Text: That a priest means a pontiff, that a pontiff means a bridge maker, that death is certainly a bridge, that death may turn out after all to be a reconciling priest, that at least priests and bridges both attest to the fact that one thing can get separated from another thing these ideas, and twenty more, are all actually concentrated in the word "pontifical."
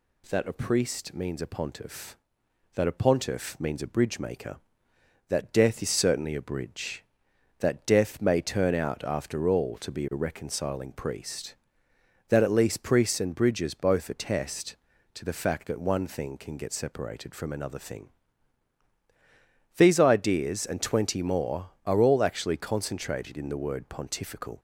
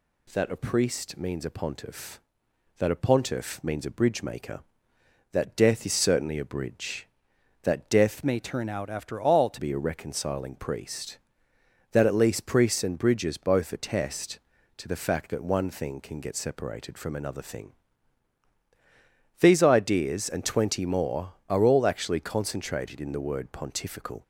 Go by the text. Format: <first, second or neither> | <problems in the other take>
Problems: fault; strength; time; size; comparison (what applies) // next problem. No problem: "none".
first | changes voice from "may" to "to"; from 8.2 to 9.5 s; 1.3 s long // pauses between "thing" and "these"; strong; at 17.7 s; 1.6 s long; strong in the first